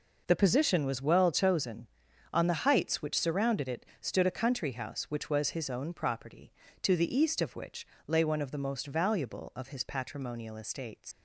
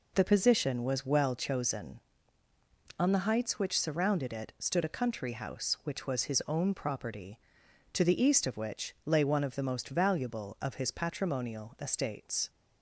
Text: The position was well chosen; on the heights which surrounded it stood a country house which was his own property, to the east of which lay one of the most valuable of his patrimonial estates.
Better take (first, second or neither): second